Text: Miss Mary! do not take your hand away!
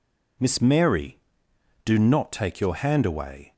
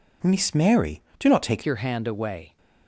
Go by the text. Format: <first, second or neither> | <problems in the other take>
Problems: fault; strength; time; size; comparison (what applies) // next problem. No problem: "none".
first | changes voice at "your"; from 1.6 s on; 0.9 s long